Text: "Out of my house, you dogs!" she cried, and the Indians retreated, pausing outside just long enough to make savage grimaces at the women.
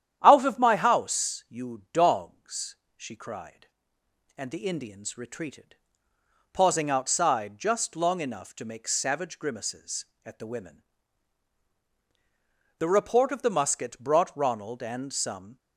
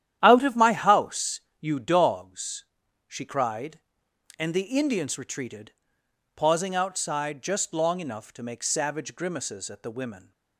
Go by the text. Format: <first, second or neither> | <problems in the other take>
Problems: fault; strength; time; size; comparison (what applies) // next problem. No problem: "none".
second | starts louder than the rest; strong; until 1.2 s; 10 dB; strong in the second // goes on to say "The report of the musket brought Ronald and some"; strong; from 12.7 s on; 2.7 s long